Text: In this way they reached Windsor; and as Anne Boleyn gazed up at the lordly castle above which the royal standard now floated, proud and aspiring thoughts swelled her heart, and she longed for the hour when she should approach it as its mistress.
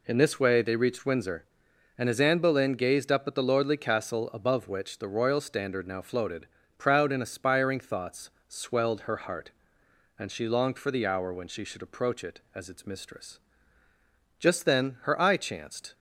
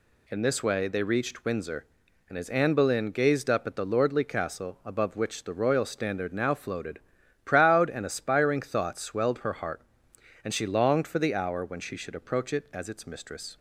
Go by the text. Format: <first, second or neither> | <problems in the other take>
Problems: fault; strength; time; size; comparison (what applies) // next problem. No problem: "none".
second | pauses between "thoughts" and "swelled"; slight; at 8.3 s; 0.16 s long // goes on to say "Just then her eye chanced"; from 14.3 s on; 1.5 s long